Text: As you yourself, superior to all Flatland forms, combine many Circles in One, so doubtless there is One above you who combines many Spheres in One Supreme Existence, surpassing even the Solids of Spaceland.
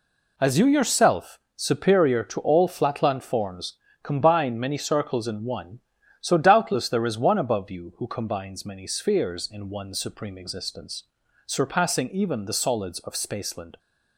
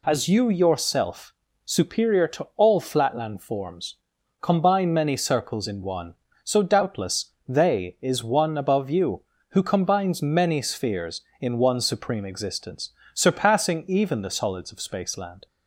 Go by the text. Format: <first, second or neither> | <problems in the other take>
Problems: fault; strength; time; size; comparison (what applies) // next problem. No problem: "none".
first | says "they" for "there"; at 7.4 s